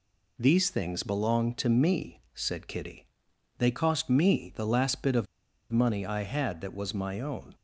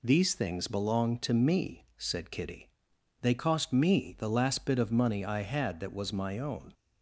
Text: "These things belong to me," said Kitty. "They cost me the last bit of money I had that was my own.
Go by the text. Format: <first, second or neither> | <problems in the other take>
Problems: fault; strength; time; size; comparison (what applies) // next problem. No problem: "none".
second | pauses between "of" and "money"; noticeable; at 5.2 s; 0.47 s long